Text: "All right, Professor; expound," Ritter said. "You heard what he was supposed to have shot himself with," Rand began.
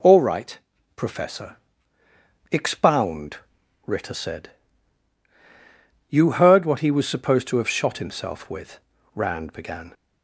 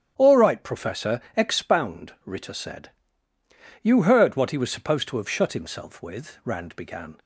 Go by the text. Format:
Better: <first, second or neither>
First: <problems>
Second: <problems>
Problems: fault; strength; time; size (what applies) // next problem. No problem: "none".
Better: first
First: none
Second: starts louder than the rest; strong; until 1.1 s; 9.5 dB // says "shut" for "shot"; at 5.2 s